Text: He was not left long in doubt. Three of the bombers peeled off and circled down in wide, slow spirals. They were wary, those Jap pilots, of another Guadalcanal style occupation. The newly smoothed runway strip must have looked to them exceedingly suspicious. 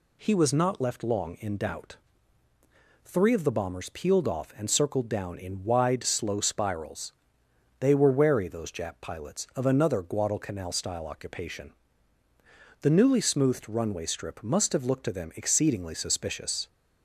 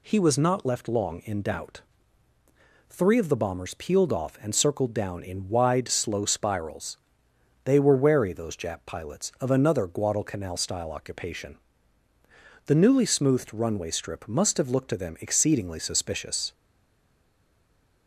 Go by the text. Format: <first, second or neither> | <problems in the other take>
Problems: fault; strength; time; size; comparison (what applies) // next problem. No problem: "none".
first | stays silent after the last word; noticeable; from 16.5 s on; 1.5 s long